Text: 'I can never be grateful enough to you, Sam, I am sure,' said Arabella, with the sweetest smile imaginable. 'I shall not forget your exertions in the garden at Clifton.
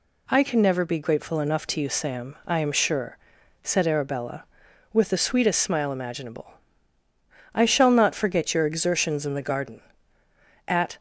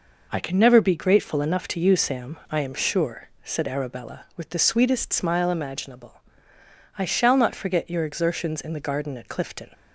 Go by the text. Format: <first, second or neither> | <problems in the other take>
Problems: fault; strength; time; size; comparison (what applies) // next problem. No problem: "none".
second | stops before "Clifton"; at 10.9 s